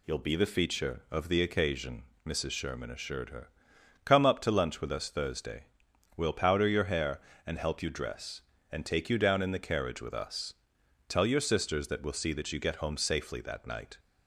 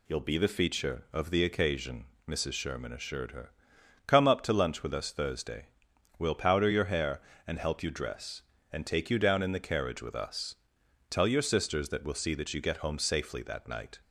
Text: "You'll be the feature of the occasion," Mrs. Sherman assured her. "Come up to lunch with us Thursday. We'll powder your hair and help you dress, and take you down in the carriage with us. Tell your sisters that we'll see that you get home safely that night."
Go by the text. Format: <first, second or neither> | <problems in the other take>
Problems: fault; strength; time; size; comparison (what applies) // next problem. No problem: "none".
neither | none